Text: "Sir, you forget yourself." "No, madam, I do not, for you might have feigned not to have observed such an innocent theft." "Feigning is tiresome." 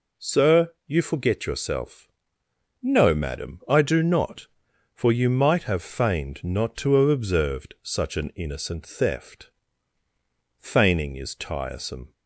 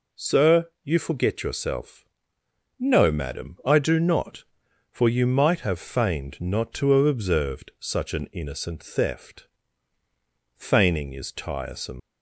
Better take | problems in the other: first | leaves "tiresome" unfinished; at 11.9 s; 100 ms

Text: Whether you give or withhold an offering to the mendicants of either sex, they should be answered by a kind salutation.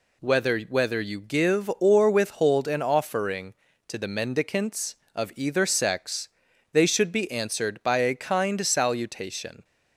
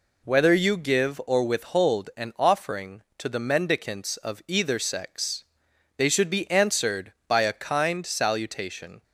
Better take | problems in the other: second | says "Whether" twice; at 0.5 s

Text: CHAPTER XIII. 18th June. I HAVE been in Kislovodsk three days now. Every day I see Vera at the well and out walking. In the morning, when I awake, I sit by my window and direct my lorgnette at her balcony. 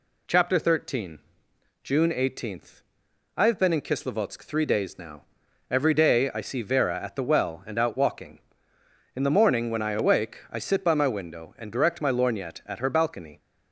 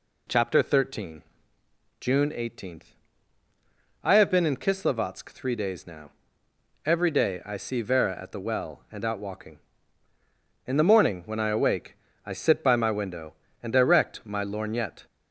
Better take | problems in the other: first | stops before "at her balcony"; at 15.0 s

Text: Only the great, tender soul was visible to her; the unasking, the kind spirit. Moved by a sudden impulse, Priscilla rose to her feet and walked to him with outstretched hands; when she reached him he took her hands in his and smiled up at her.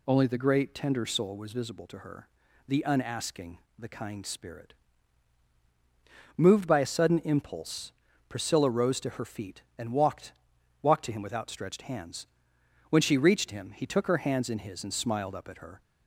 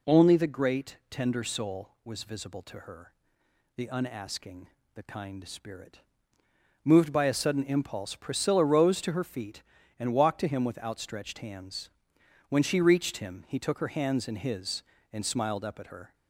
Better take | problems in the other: second | says "walked" twice; at 10.8 s

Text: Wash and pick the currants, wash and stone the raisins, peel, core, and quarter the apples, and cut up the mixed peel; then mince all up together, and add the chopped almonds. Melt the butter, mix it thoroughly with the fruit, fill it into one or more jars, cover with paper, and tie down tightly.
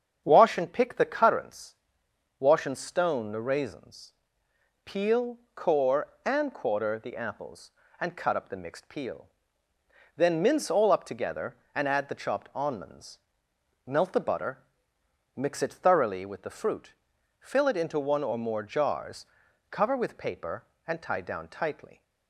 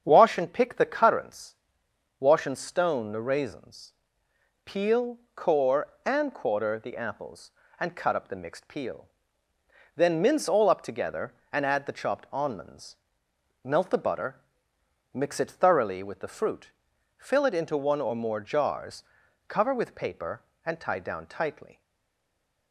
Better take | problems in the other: first | starts louder than the rest; strong; until 1.0 s; 7.5 dB; strong in the first // stays silent after the last word; from 21.8 s on; 0.9 s long

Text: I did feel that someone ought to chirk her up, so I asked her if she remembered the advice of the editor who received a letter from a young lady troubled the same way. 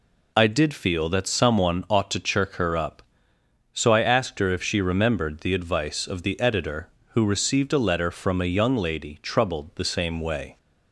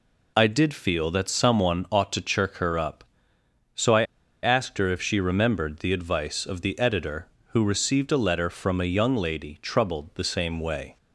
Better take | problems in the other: first | pauses between "I" and "asked"; at 4.0 s; 0.39 s long

